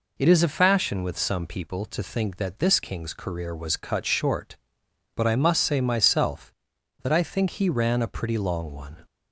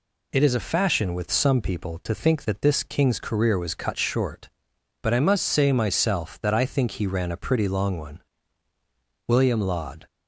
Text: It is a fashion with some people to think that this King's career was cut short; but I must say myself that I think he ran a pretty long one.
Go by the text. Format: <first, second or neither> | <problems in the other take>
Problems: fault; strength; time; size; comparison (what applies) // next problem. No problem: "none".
first | goes on to say "William Laud"; noticeable; from 9.2 s on; 0.78 s long